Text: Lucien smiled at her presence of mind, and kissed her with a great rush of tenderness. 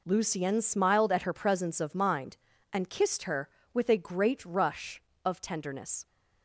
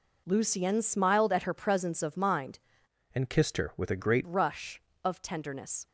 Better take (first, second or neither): first